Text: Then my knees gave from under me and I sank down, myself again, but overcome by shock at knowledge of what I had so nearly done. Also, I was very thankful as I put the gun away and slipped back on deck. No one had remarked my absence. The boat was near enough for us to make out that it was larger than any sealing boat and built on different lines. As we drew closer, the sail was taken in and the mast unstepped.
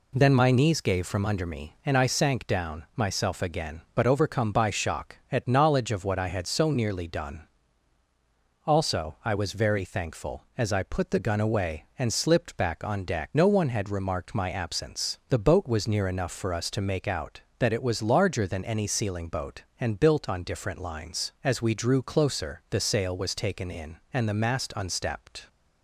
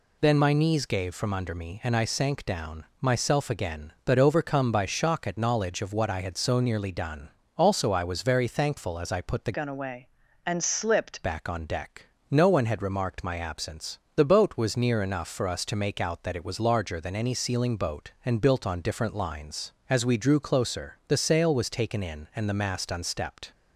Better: first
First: none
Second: changes voice from "gun" to "slipped"; from 9.5 to 11.2 s; 1.7 s long

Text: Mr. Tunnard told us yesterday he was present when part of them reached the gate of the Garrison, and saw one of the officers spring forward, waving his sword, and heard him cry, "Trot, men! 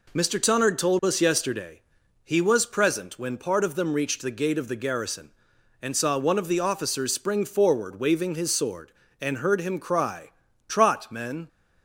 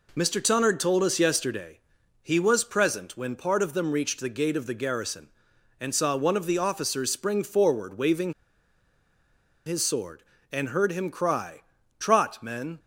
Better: first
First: pauses between "yesterday" and "he"; at 1.7 s; 0.44 s long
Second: pauses between "yesterday" and "he"; at 1.7 s; 0.44 s long // pauses between "waving" and "his"; strong; at 8.3 s; 1.3 s long

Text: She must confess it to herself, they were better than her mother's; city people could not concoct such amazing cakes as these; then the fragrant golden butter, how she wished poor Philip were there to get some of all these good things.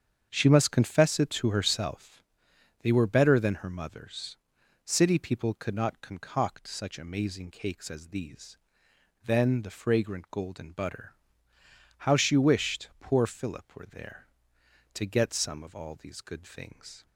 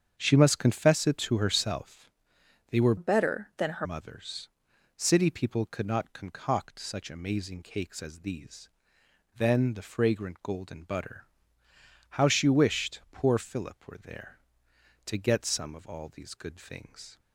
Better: first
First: starts louder than the rest; strong; until 1.3 s; 7.5 dB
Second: starts louder than the rest; strong; until 1.2 s; 7.5 dB // changes voice from "better" to "her"; from 2.9 to 3.8 s; 0.9 s long

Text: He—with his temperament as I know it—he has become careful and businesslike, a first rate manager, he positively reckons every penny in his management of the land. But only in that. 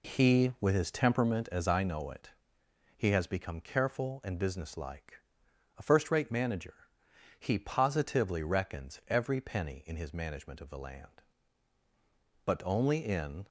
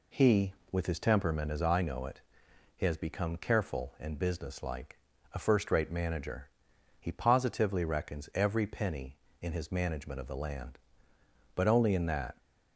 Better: second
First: stops before "that"; at 13.4 s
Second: none

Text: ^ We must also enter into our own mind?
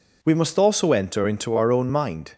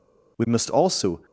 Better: first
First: none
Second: stops before "enter into our own mind"; at 1.2 s

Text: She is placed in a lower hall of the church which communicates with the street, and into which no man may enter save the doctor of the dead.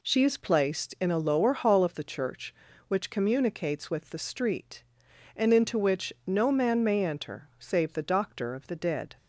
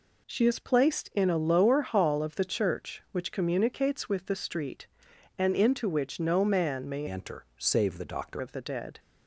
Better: first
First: none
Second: changes voice from "enter" to "doctor"; from 7.0 to 8.4 s; 1.4 s long

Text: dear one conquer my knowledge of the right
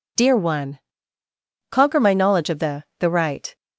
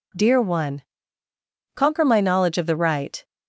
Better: second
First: pauses between "one" and "conquer"; noticeable; at 0.7 s; 0.92 s long // says "the" twice; at 2.9 s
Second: pauses between "one" and "conquer"; noticeable; at 0.8 s; 0.92 s long

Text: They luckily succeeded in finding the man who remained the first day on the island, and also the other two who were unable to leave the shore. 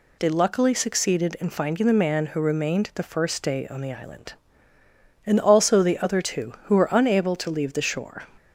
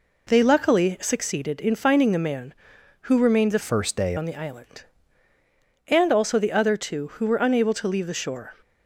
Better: first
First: none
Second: changes voice from "first" to "day"; from 3.6 to 4.1 s; 0.5 s long

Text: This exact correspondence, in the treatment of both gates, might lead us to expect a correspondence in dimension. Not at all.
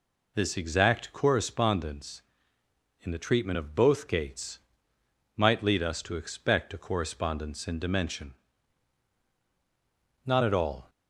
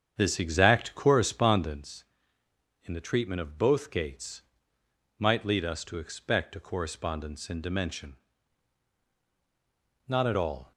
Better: first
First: none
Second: starts louder than the rest; strong; until 1.9 s; 8 dB

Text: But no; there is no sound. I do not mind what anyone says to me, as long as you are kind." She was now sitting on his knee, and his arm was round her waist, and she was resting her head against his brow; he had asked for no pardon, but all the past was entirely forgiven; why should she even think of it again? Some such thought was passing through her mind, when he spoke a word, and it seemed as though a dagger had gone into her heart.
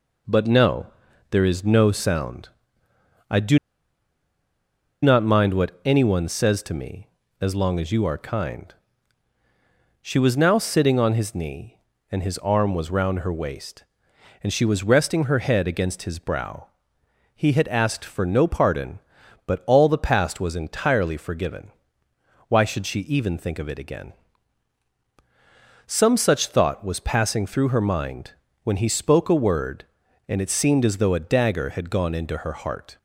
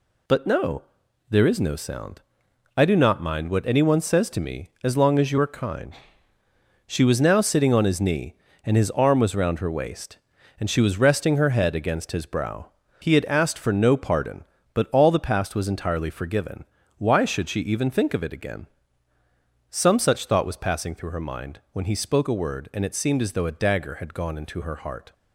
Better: second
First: pauses between "do" and "not"; strong; at 3.5 s; 1.4 s long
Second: none

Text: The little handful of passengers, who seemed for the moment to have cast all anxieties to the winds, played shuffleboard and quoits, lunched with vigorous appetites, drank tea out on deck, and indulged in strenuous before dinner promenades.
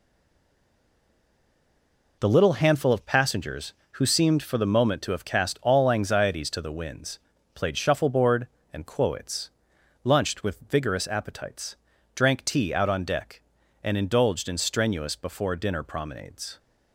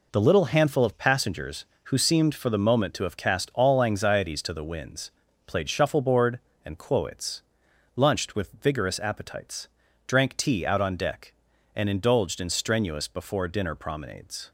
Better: second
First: stays silent before the first word; until 2.1 s; 2.1 s long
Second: none

